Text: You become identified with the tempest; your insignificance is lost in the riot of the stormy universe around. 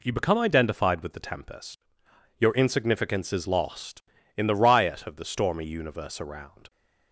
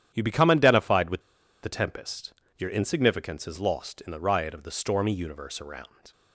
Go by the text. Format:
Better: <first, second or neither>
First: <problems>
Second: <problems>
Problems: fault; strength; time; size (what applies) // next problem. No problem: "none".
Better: first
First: none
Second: starts louder than the rest; strong; until 1.1 s; 10 dB // pauses between "with" and "the"; at 1.2 s; 0.41 s long